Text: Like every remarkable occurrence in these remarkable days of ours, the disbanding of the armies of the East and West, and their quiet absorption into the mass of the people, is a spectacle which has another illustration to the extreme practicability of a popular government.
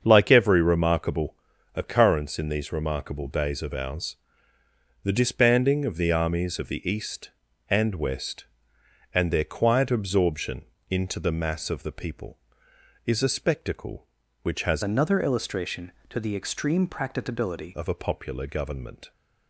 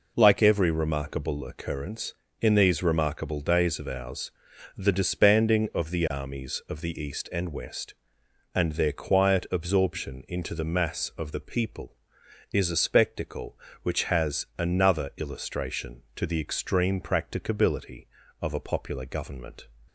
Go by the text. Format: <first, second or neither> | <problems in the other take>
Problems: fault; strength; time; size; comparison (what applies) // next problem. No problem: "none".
second | starts louder than the rest; until 1.0 s; 7 dB // pauses between "remarkable" and "occurrence"; at 1.3 s; 0.40 s long // pauses between "absorption" and "into"; slight; at 10.6 s; 0.24 s long // changes voice from "another" to "practicability"; from 14.8 to 17.7 s; 2.9 s long